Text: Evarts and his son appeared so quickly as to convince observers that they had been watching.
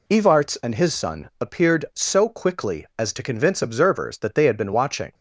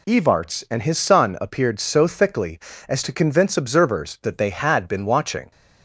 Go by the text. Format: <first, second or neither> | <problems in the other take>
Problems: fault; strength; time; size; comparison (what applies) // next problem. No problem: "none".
first | says "thickly" for "quickly"; at 2.0 s